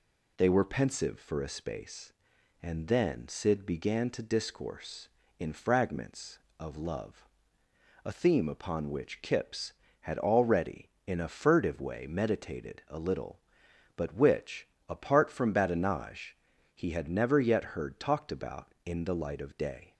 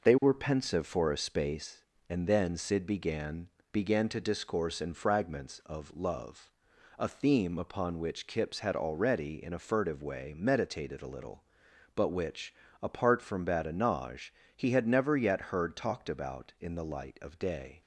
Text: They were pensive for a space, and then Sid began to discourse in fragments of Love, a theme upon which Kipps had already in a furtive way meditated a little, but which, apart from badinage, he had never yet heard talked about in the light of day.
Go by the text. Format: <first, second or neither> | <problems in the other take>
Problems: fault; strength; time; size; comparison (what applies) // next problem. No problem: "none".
first | says "began" twice; at 3.7 s